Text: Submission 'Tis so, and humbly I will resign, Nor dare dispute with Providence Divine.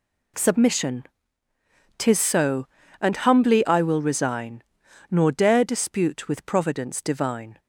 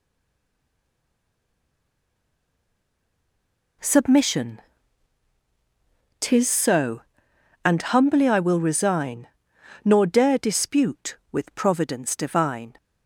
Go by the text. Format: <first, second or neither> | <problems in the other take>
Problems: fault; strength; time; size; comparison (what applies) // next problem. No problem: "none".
first | stays silent before the first word; strong; until 3.8 s; 3.8 s long // pauses between "Submission" and "Tis"; strong; at 4.6 s; 1.5 s long; noticeable in the first